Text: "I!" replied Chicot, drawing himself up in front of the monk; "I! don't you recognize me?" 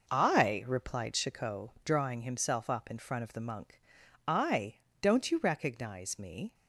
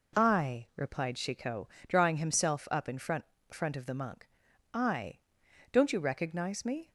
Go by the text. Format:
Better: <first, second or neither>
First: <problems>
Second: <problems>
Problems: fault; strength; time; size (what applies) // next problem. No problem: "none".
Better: first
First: none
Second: says "front" twice; at 3.5 s